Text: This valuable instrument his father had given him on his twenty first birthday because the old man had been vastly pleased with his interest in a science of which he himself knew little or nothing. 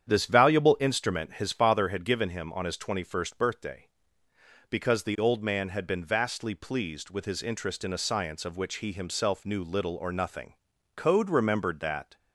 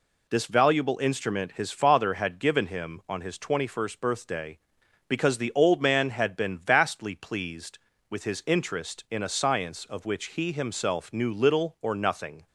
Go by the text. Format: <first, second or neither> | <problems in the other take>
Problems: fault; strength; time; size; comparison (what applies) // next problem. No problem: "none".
second | starts louder than the rest; strong; until 1.1 s; 9 dB // goes on to say "Code remembered that"; noticeable; from 10.9 s on; 1.2 s long